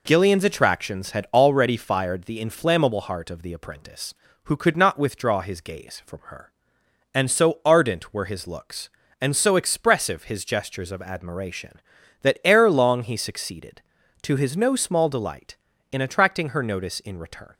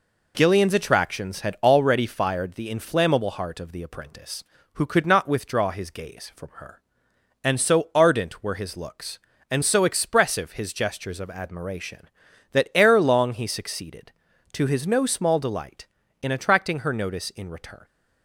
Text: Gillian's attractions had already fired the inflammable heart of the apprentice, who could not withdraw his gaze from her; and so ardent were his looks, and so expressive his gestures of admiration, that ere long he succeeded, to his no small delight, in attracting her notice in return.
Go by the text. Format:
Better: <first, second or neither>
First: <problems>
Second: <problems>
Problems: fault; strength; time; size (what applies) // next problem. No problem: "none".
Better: neither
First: none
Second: none